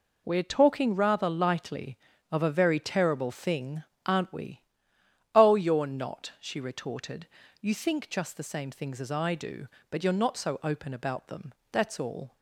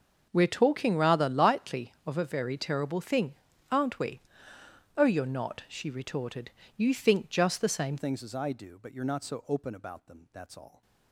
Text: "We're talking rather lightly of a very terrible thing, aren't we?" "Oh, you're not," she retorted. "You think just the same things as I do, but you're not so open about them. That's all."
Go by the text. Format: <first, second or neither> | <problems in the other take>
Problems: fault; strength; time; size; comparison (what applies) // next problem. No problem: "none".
first | starts louder than the rest; until 1.3 s; 6.5 dB // changes voice at "things"; from 7.9 s on; 2.9 s long